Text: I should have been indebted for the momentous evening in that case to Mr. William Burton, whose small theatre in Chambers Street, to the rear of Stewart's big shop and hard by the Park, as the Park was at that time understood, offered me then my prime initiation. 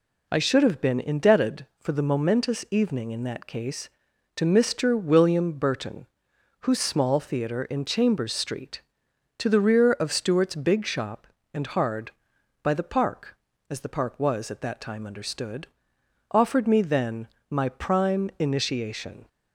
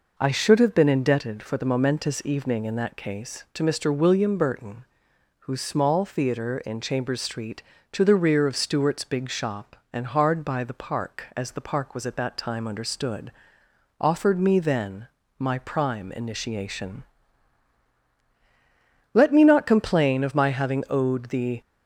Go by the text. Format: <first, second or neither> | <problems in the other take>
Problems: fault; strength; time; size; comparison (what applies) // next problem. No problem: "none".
first | pauses between "then" and "my"; slight; at 15.0 s; 0.30 s long; slight in the first // goes on to say "Let me not complain of my having owed the"; strong; from 19.1 s on; 2.4 s long